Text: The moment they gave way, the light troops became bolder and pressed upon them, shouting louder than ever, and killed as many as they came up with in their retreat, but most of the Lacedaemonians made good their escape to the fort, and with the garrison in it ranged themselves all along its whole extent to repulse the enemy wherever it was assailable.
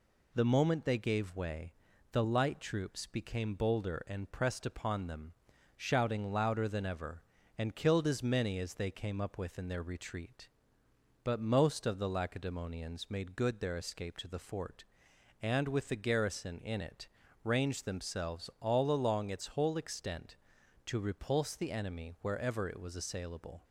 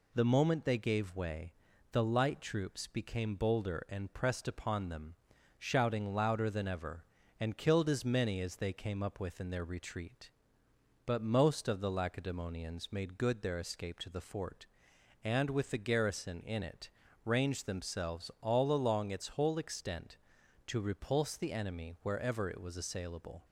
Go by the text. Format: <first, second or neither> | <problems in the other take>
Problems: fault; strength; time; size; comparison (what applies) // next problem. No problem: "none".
neither | pauses between "it" and "ranged"; slight; the same in both